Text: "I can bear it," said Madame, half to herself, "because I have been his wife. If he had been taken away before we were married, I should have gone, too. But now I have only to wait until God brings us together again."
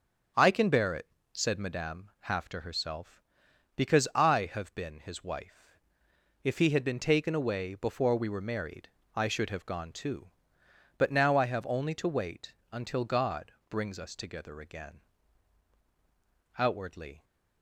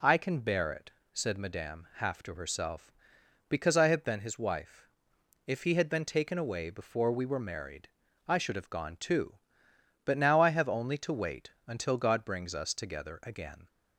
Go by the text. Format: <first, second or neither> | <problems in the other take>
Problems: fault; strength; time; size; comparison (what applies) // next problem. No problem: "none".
second | starts louder than the rest; strong; until 1.6 s; 7.5 dB // pauses between "wait" and "until"; slight; at 12.5 s; 0.18 s long; slight in the second // pauses between "God" and "brings"; slight; at 13.5 s; 0.16 s long // goes on to say "Outwardly"; noticeable; from 16.5 s on; 0.66 s long